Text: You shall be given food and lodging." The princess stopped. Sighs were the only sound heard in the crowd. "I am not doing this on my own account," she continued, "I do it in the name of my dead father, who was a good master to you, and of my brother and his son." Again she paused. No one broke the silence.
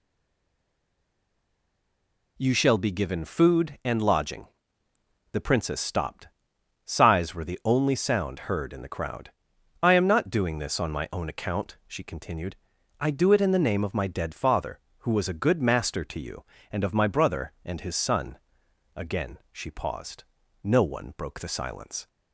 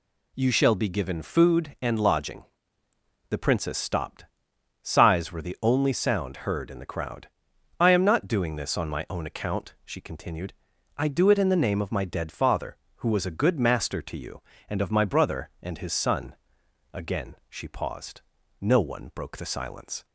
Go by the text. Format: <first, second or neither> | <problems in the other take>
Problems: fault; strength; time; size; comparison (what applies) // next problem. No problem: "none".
second | stays silent before the first word; until 2.3 s; 2.3 s long